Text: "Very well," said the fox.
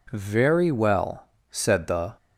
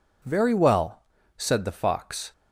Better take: second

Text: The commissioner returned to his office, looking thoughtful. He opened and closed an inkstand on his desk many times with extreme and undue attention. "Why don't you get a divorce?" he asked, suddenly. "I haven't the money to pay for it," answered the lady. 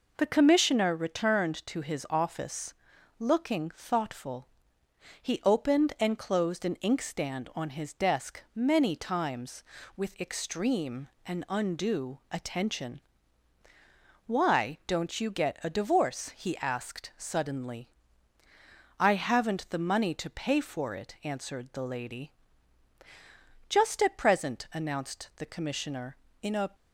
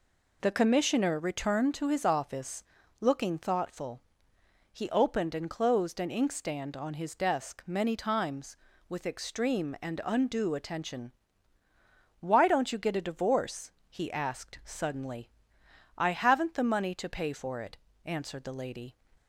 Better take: second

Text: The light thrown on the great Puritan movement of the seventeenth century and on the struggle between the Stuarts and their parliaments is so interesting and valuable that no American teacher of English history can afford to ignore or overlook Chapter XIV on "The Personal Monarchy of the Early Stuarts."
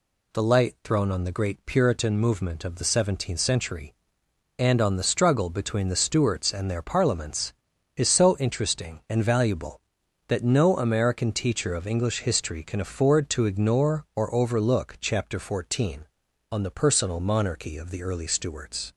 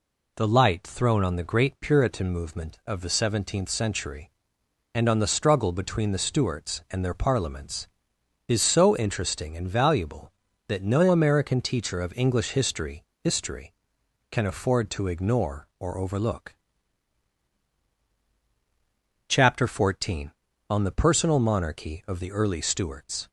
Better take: first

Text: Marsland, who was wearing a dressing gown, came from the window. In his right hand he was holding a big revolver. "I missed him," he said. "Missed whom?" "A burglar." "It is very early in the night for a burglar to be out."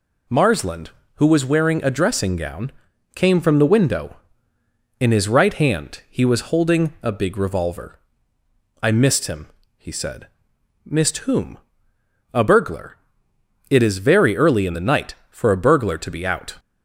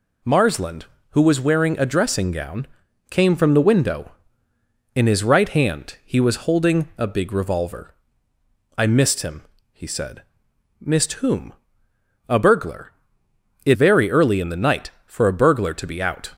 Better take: first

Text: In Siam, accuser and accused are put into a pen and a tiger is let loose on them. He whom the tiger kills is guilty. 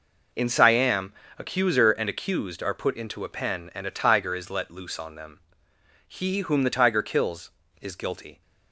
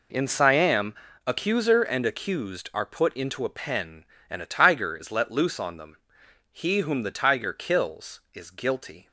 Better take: neither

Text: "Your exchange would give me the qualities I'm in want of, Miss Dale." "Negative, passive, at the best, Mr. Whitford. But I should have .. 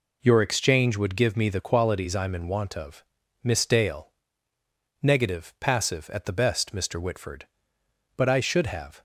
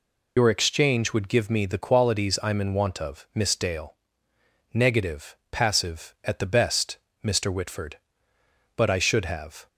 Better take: first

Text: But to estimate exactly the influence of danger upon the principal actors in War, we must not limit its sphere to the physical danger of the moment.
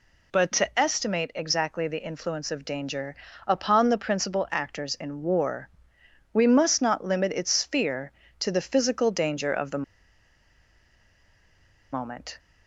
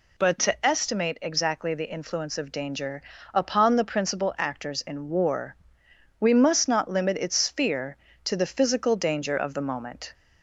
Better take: second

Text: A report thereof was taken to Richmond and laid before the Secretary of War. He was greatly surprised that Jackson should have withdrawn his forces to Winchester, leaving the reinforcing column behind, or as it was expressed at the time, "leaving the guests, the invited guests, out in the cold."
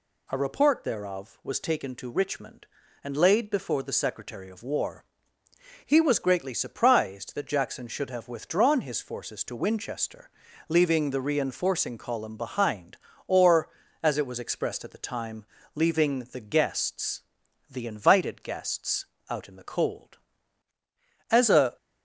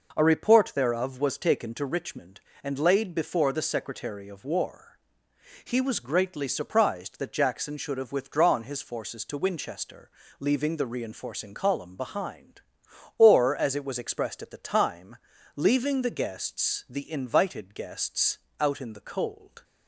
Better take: second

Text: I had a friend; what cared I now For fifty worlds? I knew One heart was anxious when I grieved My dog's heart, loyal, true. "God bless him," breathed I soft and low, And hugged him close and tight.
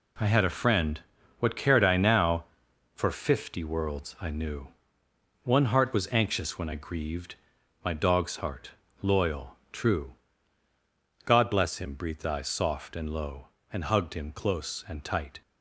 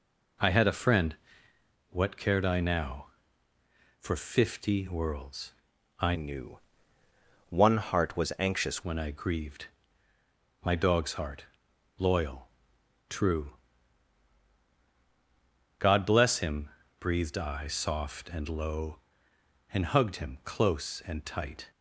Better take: first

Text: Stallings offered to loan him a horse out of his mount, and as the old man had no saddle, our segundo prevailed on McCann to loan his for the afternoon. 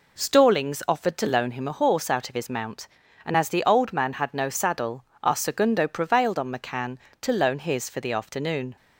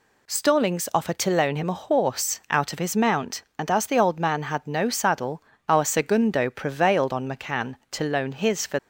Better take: first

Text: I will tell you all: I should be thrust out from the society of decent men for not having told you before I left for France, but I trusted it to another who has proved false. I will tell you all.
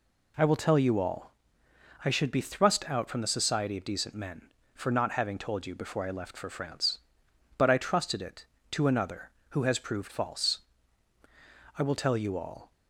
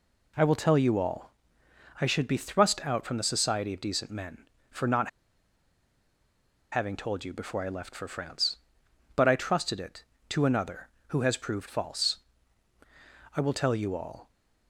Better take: first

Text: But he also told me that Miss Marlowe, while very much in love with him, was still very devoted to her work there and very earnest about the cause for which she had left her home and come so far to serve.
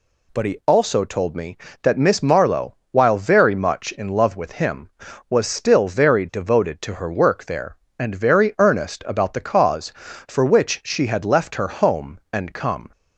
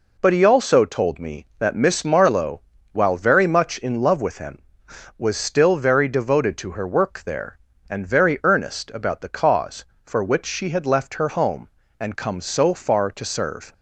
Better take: second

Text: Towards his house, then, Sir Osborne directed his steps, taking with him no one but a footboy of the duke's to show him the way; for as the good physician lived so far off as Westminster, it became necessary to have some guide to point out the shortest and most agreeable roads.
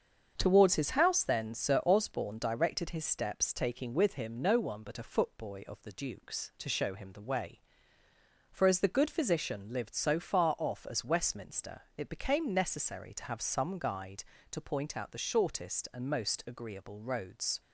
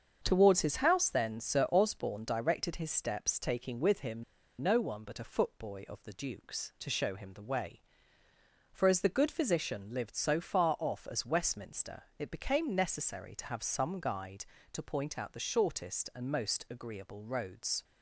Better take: first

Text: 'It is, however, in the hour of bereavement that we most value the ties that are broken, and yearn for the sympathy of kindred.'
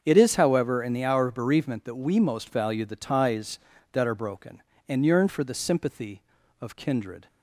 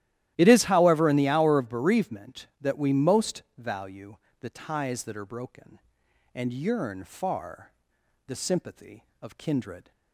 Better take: first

